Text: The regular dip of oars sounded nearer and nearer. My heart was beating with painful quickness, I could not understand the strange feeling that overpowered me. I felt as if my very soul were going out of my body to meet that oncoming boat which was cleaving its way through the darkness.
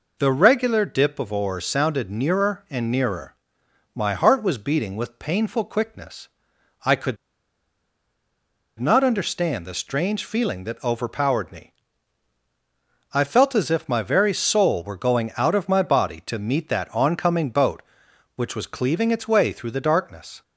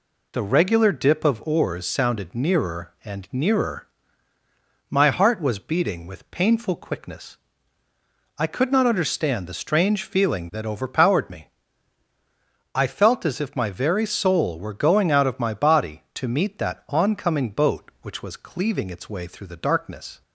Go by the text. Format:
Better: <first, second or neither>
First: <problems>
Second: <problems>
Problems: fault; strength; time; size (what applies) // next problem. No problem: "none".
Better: second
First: pauses between "could" and "not"; strong; at 7.1 s; 1.6 s long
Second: none